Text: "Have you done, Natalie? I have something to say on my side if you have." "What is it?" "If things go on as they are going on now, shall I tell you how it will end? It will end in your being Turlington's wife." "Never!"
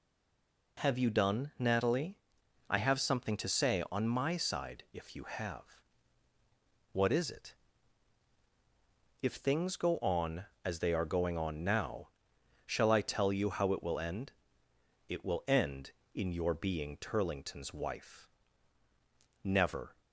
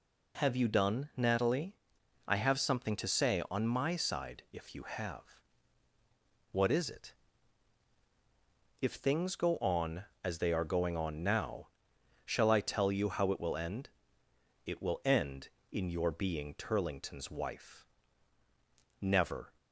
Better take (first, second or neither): second